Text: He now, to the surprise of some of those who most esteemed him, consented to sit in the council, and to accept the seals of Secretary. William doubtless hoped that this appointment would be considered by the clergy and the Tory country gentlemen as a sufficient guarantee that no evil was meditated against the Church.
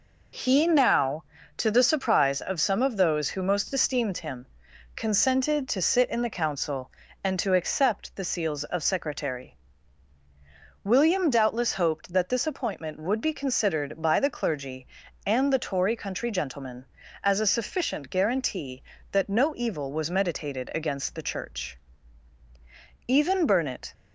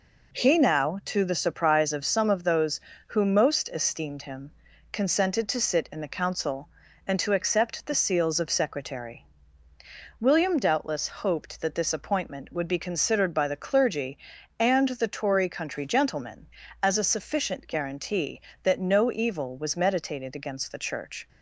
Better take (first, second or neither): second